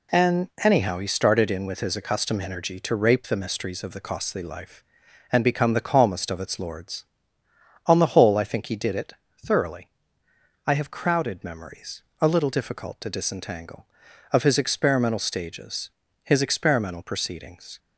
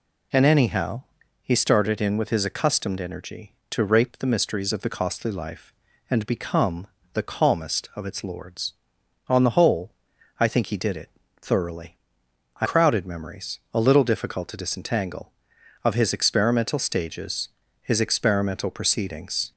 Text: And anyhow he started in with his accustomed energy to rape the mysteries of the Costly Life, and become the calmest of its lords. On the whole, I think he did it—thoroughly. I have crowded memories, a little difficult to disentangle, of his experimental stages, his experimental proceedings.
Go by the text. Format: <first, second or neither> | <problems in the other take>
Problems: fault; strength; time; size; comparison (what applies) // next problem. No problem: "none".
first | pauses between "anyhow" and "he"; at 1.0 s; 0.40 s long // pauses between "become" and "the"; slight; at 6.8 s; 0.28 s long // skips "have"; at 12.6 s